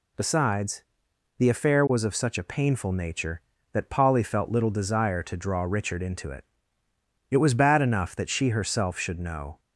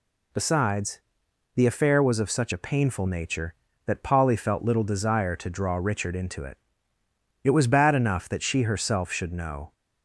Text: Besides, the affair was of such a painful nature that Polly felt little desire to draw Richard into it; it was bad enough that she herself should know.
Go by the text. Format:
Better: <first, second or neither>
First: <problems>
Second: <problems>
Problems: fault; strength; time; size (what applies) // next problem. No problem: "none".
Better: neither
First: none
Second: none